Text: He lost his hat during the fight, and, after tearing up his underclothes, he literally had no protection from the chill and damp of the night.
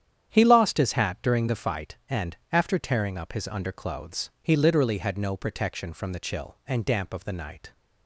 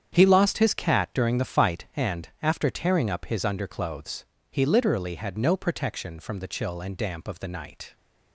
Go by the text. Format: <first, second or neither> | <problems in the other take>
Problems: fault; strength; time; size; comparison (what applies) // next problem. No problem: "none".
first | starts louder than the rest; strong; until 1.1 s; 8.5 dB; strong in the first // says "cat" for "hat"; at 0.7 s